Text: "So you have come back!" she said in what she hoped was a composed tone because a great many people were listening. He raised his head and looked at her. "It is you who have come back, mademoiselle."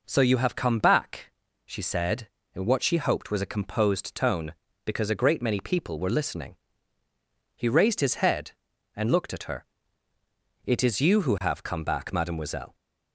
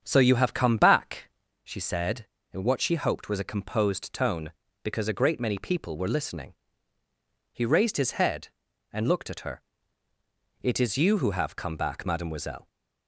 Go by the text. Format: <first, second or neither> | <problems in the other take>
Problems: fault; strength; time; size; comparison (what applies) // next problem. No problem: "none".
first | starts louder than the rest; strong; until 1.6 s; 7.5 dB